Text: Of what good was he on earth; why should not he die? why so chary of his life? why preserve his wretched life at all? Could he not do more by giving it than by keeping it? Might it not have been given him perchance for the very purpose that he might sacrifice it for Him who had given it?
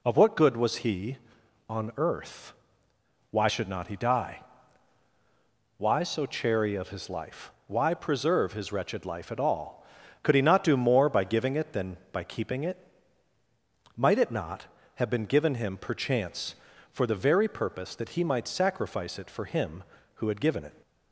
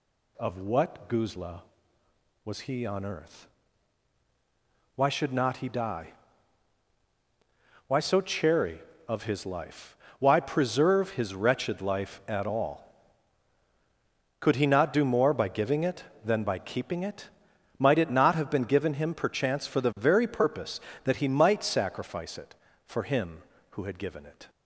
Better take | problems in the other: first | says "guzla" for "good"; at 1.0 s

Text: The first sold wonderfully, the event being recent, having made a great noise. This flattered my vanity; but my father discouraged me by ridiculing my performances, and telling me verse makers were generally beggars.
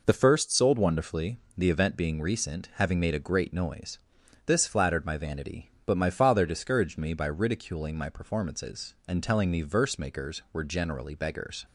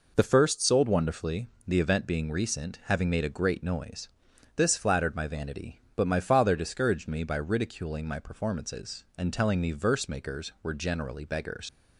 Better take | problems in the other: first | leaves "beggars" unfinished; at 11.6 s; 60 ms

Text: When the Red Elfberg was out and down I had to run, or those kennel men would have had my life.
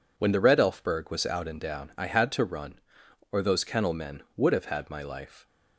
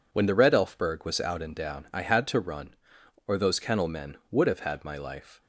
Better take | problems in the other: neither | none

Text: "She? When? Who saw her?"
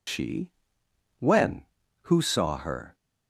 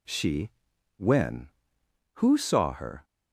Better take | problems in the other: second | loses the start of "She"; at 0.0 s; 100 ms

